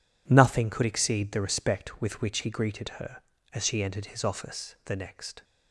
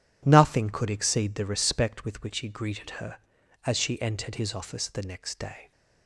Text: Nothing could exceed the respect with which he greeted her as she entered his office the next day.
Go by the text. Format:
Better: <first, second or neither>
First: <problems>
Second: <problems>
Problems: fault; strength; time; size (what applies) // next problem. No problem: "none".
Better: second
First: stops before "day"; at 5.4 s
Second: none